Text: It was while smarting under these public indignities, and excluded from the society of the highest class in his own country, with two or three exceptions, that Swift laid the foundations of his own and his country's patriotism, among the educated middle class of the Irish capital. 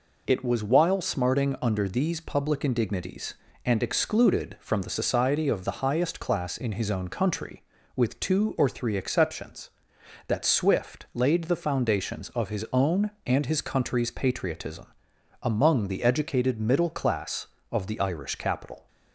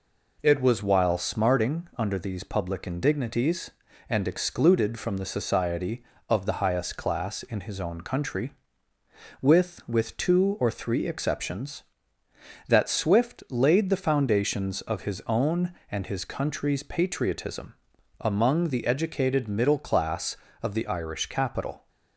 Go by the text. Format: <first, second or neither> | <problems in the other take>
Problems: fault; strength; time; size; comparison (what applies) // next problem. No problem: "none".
first | says "with" twice; at 9.8 s